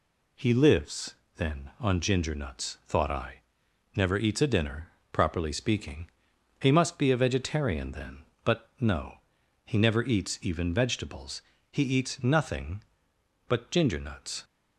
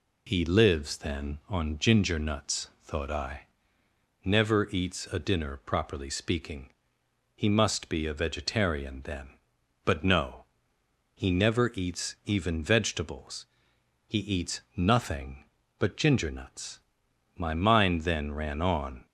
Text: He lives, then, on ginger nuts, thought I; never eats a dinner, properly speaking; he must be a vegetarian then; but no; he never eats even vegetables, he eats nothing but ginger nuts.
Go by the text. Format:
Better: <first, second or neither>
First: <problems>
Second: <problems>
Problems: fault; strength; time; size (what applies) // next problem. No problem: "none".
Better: first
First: none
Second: pauses between "eats" and "nothing"; slight; at 14.5 s; 0.16 s long // goes on to say "My mind then ran on"; strong; from 17.3 s on; 1.6 s long